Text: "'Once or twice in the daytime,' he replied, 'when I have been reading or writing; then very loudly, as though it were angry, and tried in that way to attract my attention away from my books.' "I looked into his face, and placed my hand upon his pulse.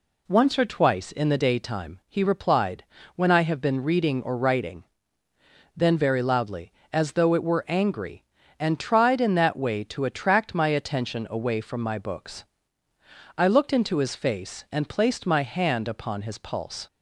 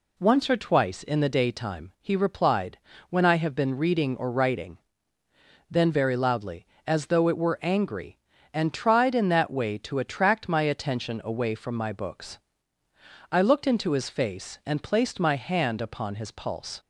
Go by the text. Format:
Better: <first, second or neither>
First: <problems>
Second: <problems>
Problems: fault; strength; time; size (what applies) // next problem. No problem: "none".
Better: neither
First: none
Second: none